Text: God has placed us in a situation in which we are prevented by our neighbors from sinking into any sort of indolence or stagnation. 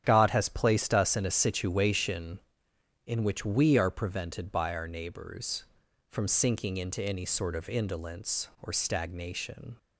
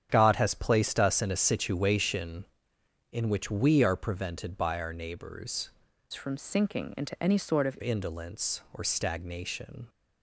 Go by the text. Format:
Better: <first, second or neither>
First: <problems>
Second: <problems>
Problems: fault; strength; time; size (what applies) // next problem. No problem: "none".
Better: first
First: starts louder than the rest; strong; until 1.0 s; 9.5 dB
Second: starts louder than the rest; strong; until 1.1 s; 9 dB // changes voice from "from" to "of"; from 6.1 to 7.7 s; 1.6 s long